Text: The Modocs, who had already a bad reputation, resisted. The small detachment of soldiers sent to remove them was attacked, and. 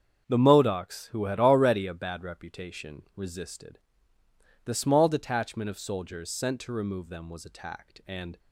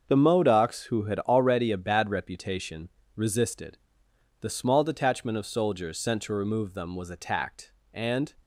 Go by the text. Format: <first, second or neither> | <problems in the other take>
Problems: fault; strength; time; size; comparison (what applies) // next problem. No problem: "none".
neither | starts louder than the rest; the same in both